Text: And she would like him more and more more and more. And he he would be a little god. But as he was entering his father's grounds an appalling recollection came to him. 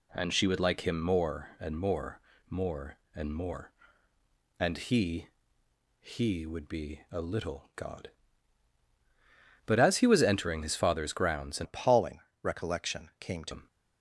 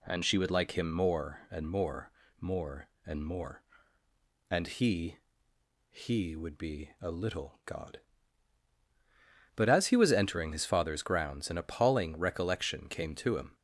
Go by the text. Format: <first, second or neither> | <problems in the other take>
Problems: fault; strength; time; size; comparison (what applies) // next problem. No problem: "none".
second | pauses between "more" and "more"; slight; at 2.1 s; 0.32 s long; slight in the second // pauses between "he" and "he"; noticeable; at 5.2 s; 0.74 s long; noticeable in the second // changes voice from "appalling" to "to"; from 11.6 to 13.5 s; 1.9 s long // pauses between "appalling" and "recollection"; slight; at 12.1 s; 0.22 s long